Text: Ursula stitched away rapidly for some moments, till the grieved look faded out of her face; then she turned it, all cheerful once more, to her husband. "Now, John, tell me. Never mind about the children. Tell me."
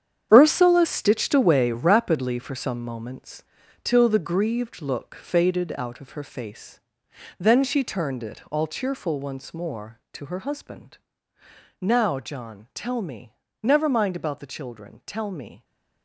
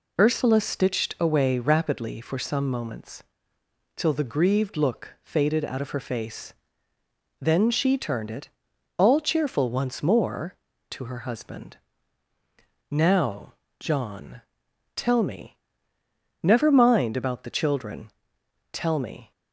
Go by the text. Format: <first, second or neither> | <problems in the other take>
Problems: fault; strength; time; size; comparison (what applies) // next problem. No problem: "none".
second | gets quieter; strong; throughout; 10.5 dB